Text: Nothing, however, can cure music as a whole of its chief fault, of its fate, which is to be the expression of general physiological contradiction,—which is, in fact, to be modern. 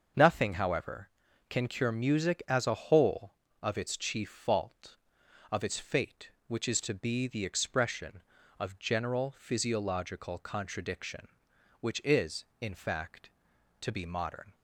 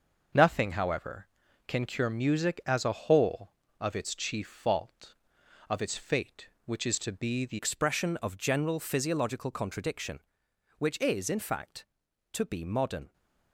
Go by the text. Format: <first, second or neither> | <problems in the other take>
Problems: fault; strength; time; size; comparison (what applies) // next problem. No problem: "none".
first | starts louder than the rest; until 1.7 s; 6 dB; also in the first // changes voice at "expression"; from 7.5 s on; 5.6 s long